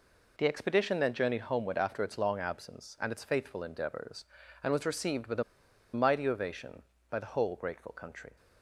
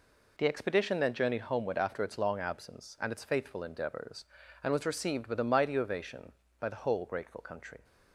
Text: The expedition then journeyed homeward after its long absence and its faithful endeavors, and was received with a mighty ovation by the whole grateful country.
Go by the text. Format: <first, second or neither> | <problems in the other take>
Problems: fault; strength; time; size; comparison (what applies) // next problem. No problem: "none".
second | pauses between "a" and "mighty"; noticeable; at 5.4 s; 0.50 s long